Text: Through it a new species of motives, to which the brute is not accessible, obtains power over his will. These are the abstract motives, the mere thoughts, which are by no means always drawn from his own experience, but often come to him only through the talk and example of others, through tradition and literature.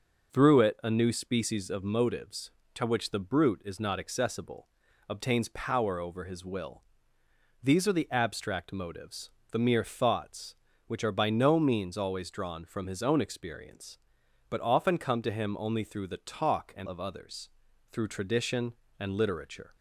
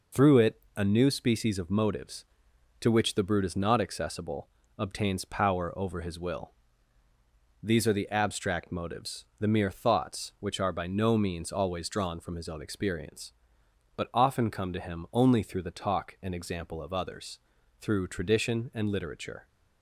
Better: second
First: starts louder than the rest; noticeable; until 1.3 s; 6 dB // skips "example"; at 16.8 s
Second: none

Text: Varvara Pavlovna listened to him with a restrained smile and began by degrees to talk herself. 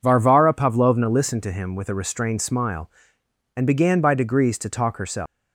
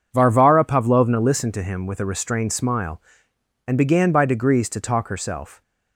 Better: second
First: leaves "herself" unfinished; at 5.2 s; 245 ms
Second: none

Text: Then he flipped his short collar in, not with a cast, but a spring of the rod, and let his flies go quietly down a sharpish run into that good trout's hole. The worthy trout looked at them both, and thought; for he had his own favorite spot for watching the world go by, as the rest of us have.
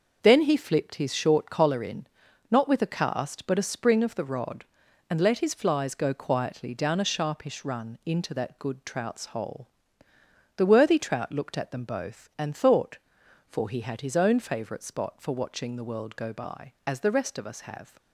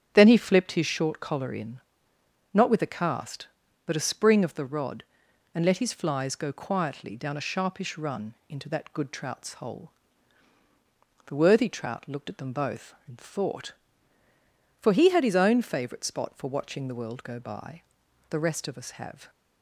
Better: first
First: starts louder than the rest; noticeable; until 1.2 s; 6 dB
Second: starts louder than the rest; strong; until 1.1 s; 8.5 dB // pauses between "run" and "into"; slight; at 8.3 s; 0.16 s long // skips "as"; at 18.0 s

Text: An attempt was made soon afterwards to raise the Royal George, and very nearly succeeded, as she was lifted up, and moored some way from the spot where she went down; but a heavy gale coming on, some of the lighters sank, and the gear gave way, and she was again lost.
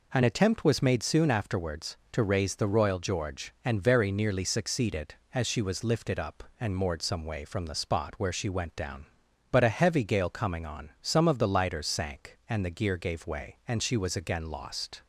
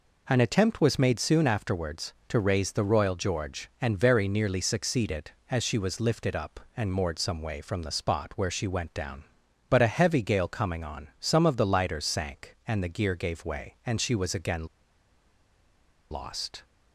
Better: first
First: none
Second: pauses between "again" and "lost"; strong; at 14.6 s; 1.4 s long

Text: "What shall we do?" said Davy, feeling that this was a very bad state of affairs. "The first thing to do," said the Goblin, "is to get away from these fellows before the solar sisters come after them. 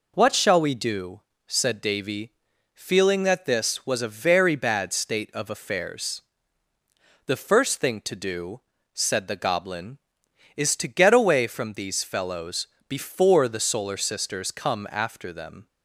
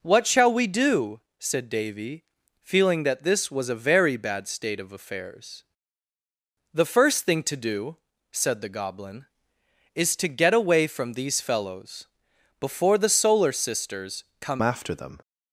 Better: first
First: pauses between "fellows" and "before"; slight; at 12.6 s; 0.22 s long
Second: pauses between "fellows" and "before"; noticeable; at 12.0 s; 0.52 s long // pauses between "sisters" and "come"; slight; at 14.2 s; 0.16 s long // changes voice at "after"; from 14.6 s on; 0.5 s long

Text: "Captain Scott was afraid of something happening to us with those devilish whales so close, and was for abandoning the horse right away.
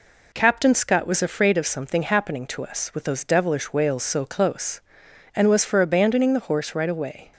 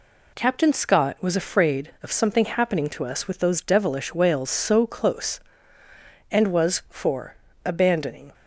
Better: first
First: none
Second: pauses between "for" and "abandoning"; slight; at 7.3 s; 0.28 s long // stops before "the horse right away"; at 8.3 s

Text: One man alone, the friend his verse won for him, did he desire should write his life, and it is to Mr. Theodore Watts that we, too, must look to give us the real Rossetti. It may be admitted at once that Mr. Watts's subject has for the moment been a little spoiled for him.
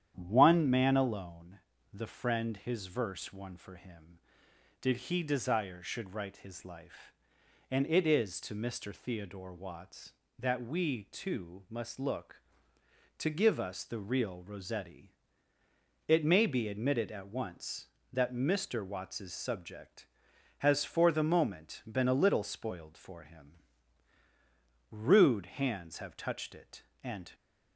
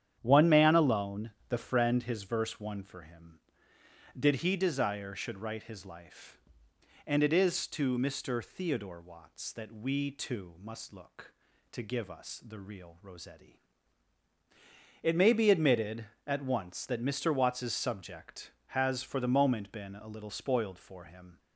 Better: second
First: starts louder than the rest; strong; until 1.1 s; 9.5 dB // goes on to say "Rude hands have touched it and"; strong; from 24.8 s on; 2.4 s long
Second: starts louder than the rest; strong; until 1.2 s; 9.5 dB

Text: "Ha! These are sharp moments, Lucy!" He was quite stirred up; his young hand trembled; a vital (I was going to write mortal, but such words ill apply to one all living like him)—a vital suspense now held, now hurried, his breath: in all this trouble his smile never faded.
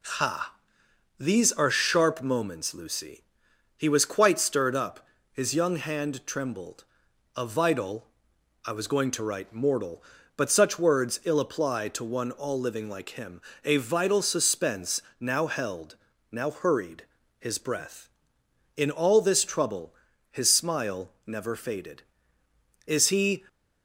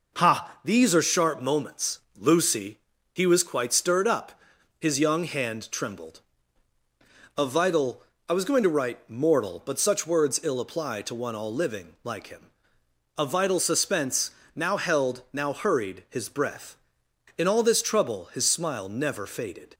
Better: second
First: pauses between "suspense" and "now"; slight; at 15.0 s; 0.18 s long // pauses between "trouble" and "his"; at 19.9 s; 0.38 s long // goes on to say "Is he"; from 22.8 s on; 0.56 s long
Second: pauses between "suspense" and "now"; slight; at 14.2 s; 0.24 s long

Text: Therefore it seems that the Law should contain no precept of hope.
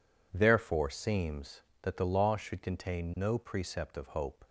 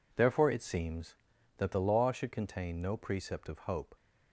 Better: second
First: skips "it"; at 0.9 s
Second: none

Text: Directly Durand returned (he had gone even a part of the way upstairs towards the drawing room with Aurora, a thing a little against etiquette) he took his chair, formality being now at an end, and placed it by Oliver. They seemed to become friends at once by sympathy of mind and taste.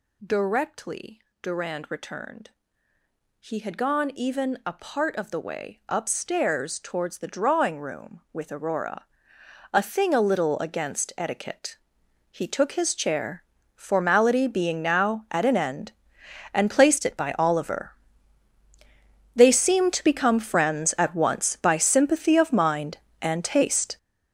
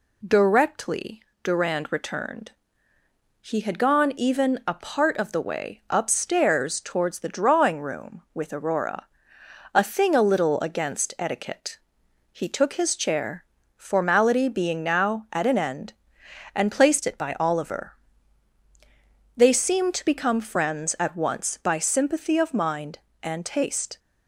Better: second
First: gets louder; strong; throughout; 11 dB // pauses between "Directly" and "Durand"; slight; at 1.2 s; 0.22 s long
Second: pauses between "Directly" and "Durand"; slight; at 1.2 s; 0.22 s long

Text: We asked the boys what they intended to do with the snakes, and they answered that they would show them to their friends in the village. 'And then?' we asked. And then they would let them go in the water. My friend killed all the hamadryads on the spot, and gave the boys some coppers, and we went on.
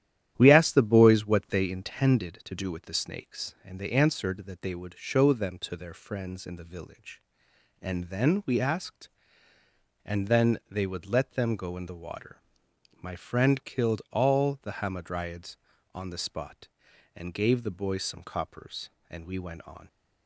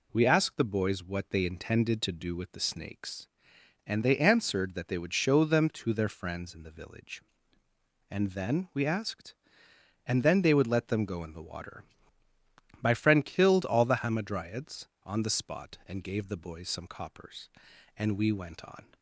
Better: second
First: starts louder than the rest; strong; until 1.9 s; 11.5 dB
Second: none

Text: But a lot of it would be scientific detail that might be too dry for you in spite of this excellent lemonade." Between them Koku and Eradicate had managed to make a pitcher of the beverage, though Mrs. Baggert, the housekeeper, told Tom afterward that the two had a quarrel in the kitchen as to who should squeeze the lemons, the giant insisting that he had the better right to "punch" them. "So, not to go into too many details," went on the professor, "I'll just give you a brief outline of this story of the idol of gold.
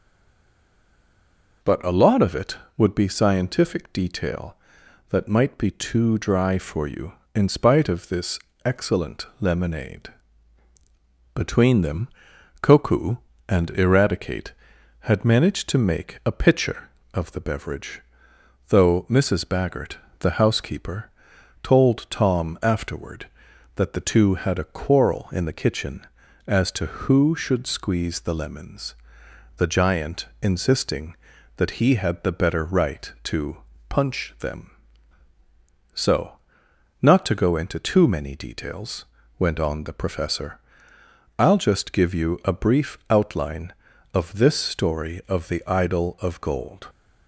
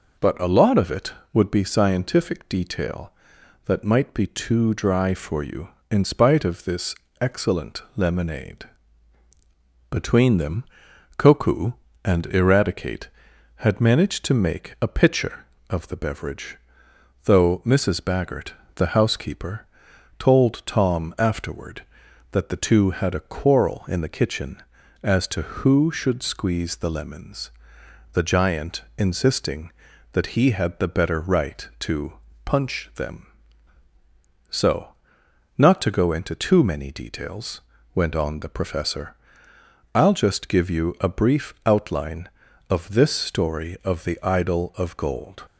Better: second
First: stays silent before the first word; noticeable; until 1.6 s; 1.6 s long // pauses between "this" and "excellent"; slight; at 8.3 s; 0.26 s long // pauses between "them" and "Koku"; noticeable; at 12.0 s; 0.54 s long // pauses between "giant" and "insisting"; slight; at 30.2 s; 0.16 s long // pauses between "to" and "punch"; slight; at 33.5 s; 0.30 s long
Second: pauses between "this" and "excellent"; slight; at 6.9 s; 0.26 s long // pauses between "them" and "Koku"; noticeable; at 10.6 s; 0.54 s long // pauses between "giant" and "insisting"; slight; at 28.8 s; 0.16 s long // pauses between "to" and "punch"; slight; at 32.1 s; 0.30 s long

